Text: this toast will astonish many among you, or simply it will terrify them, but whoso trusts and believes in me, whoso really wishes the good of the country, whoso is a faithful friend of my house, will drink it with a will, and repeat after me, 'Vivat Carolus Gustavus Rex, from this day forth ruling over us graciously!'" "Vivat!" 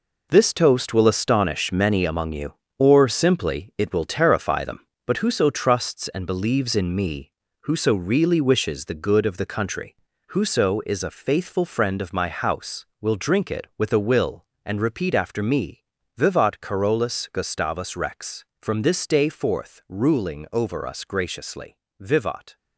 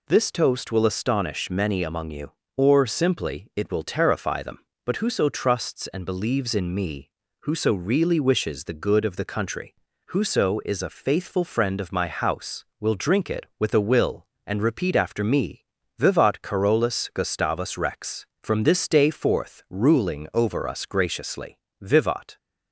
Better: second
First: gets quieter; strong; throughout; 9.5 dB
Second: none

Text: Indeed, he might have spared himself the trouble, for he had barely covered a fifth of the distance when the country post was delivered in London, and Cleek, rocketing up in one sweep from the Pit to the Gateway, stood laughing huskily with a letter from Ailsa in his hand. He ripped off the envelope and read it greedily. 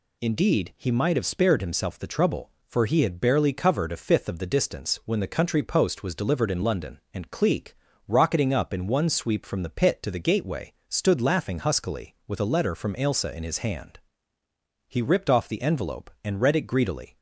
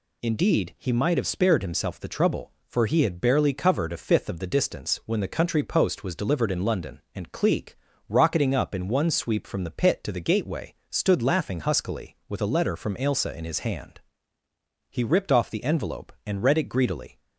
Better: neither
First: none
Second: none

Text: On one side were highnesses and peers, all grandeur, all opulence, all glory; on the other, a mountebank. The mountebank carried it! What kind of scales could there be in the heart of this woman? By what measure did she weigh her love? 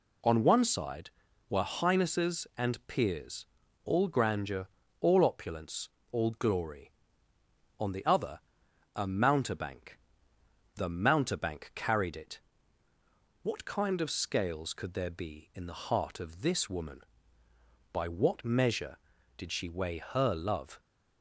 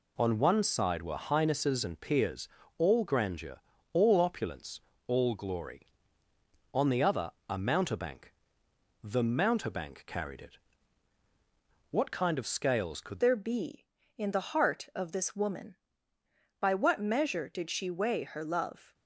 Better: first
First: none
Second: changes voice at "there"; from 13.2 s on; 5.7 s long

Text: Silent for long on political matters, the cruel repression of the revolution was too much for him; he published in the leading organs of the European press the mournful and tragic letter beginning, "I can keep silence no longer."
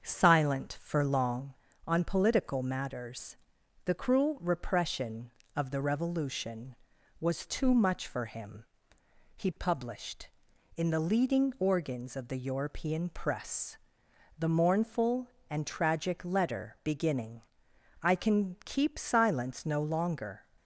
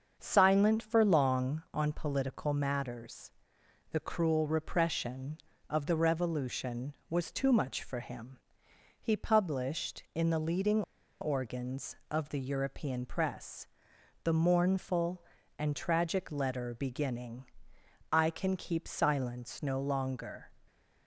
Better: first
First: starts louder than the rest; until 1.0 s; 7 dB // pauses between "press" and "the"; noticeable; at 13.7 s; 0.60 s long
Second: starts louder than the rest; until 1.2 s; 7 dB // pauses between "leading" and "organs"; at 10.8 s; 0.39 s long // pauses between "press" and "the"; noticeable; at 13.6 s; 0.56 s long

